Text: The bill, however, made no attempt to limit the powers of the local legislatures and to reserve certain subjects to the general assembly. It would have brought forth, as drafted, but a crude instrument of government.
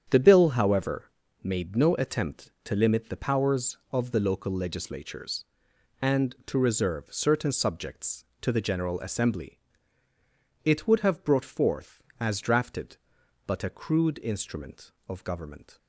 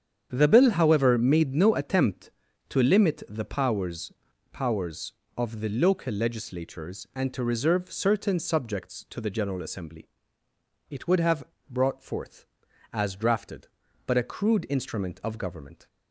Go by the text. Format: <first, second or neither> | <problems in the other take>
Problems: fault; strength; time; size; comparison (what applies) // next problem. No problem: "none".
first | starts louder than the rest; strong; until 1.3 s; 8 dB; strong in the first // says "powers" twice; at 4.5 s // pauses between "have" and "brought"; slight; at 11.4 s; 0.24 s long